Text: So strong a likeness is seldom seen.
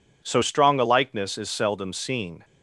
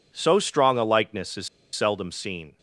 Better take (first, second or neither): first